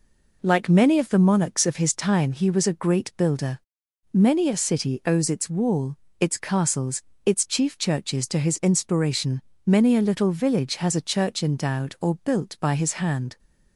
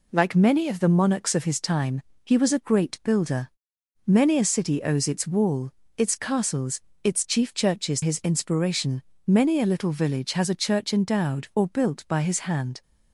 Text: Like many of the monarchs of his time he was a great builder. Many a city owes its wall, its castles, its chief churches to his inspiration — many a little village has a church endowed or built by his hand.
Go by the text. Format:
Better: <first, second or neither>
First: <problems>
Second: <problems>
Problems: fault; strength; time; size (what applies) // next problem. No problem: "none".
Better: first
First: none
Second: pauses between "time" and "he"; slight; at 2.0 s; 0.24 s long // skips "to"; at 8.0 s